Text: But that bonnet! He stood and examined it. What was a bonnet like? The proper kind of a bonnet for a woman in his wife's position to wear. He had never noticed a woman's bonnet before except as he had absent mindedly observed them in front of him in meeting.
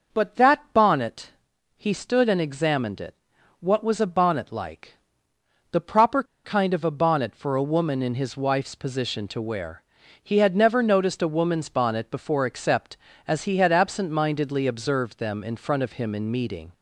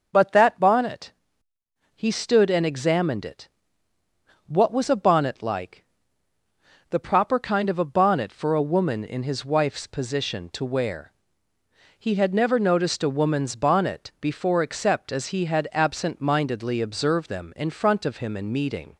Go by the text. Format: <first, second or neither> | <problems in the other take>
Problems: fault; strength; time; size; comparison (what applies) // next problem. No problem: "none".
second | pauses between "proper" and "kind"; slight; at 6.2 s; 0.20 s long